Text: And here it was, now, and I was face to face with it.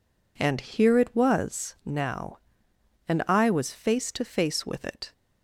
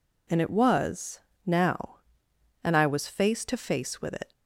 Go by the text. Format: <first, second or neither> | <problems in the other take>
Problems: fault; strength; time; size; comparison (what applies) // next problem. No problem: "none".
first | skips "here"; at 0.4 s